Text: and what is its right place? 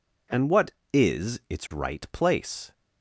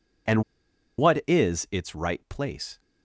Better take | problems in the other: first | pauses between "and" and "what"; noticeable; at 0.4 s; 0.55 s long

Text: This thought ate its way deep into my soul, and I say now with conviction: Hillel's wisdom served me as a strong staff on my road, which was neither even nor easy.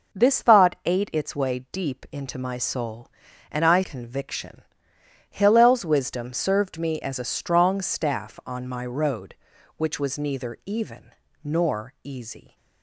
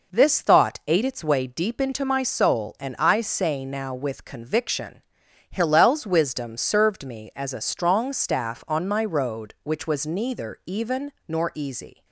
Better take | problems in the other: second | starts louder than the rest; noticeable; until 1.2 s; 6 dB // skips "say now with"; at 3.8 s // pauses between "even" and "nor"; slight; at 11.1 s; 0.32 s long; slight in the second

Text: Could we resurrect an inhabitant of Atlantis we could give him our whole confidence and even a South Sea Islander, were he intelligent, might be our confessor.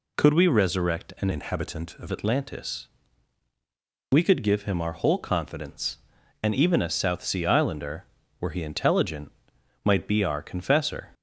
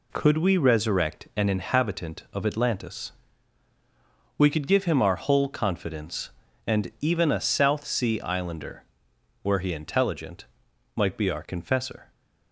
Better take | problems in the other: second | changes voice from "inhabitant" to "of"; from 1.3 to 2.0 s; 0.7 s long // pauses between "Atlantis" and "we"; at 2.8 s; 1.2 s long; also in the second

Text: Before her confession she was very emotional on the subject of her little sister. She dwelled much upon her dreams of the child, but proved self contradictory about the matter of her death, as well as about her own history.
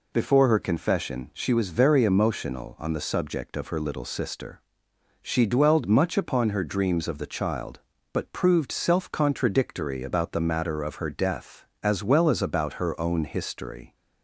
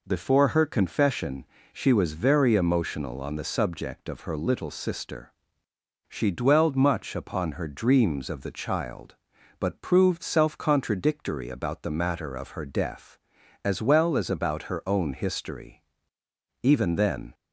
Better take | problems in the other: first | pauses between "confession" and "she"; slight; at 1.4 s; 0.28 s long // goes on to say "Even then"; noticeable; from 16.6 s on; 0.72 s long

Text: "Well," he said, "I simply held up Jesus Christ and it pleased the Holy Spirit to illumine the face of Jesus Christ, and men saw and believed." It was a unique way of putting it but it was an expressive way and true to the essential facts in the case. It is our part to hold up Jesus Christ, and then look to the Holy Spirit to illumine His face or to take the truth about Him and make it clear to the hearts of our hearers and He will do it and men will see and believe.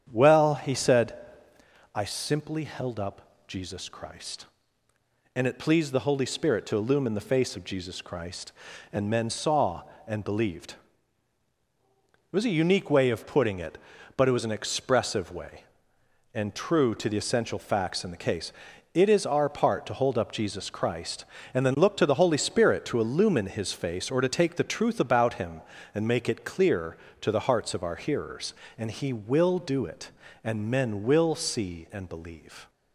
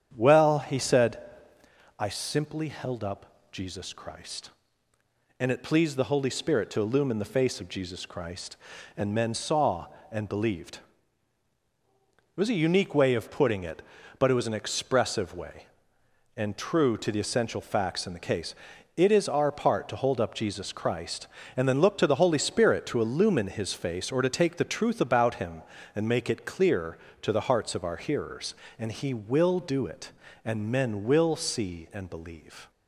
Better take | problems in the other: neither | starts louder than the rest; strong; the same in both

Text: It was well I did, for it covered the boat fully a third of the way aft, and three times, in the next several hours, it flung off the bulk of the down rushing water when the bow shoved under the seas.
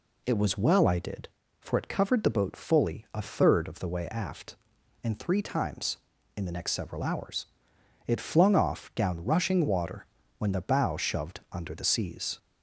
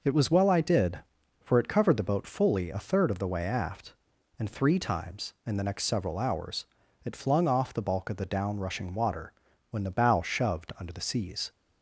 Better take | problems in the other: second | skips "the bulk of the"; at 8.9 s // pauses between "water" and "when"; slight; at 10.0 s; 0.32 s long; also in the second

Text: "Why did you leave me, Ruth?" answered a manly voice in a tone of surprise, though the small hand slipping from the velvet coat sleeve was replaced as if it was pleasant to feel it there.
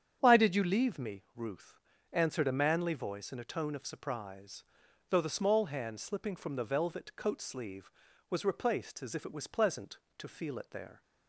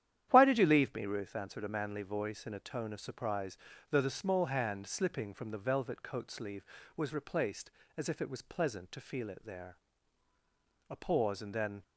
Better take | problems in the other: first | starts louder than the rest; strong; until 1.3 s; 10.5 dB; strong in the first // goes on to say "A pause and then"; noticeable; from 10.8 s on; 0.94 s long

